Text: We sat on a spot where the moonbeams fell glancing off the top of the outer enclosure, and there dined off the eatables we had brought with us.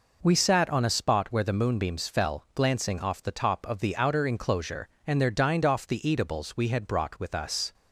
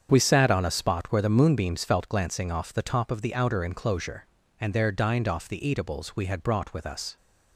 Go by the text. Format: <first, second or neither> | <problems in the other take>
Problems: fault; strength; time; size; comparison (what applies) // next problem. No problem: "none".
first | starts louder than the rest; strong; until 1.1 s; 7.5 dB // says "felt" for "fell"; at 1.8 s